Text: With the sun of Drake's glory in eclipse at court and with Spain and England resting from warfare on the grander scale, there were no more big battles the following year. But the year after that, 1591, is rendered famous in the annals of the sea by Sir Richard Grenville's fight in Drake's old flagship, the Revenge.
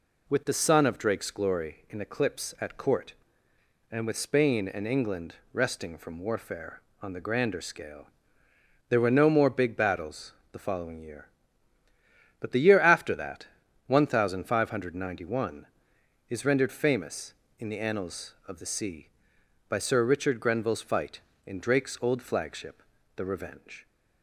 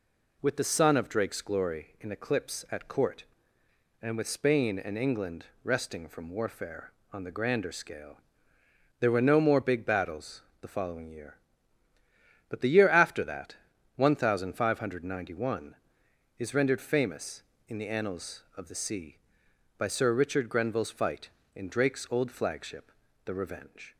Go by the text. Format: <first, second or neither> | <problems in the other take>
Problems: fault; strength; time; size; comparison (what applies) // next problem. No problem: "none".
neither | pauses between "England" and "resting"; slight; the same in both // pauses between "battles" and "the"; slight; the same in both